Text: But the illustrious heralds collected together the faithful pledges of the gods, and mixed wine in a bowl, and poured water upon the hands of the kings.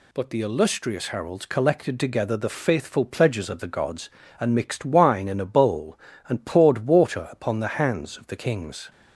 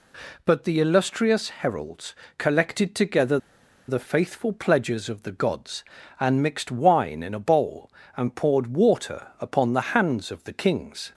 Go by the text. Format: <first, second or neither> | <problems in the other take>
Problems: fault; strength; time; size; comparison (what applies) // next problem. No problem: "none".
first | pauses between "heralds" and "collected"; slight; at 2.1 s; 0.22 s long // pauses between "together" and "the"; noticeable; at 3.3 s; 0.50 s long